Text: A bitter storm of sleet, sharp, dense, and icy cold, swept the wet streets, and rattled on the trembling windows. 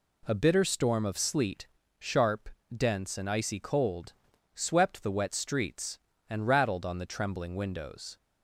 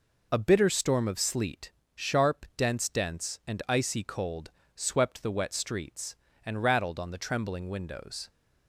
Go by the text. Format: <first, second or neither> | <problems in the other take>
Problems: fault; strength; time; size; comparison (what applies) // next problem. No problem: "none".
first | says "dense" twice; at 2.8 s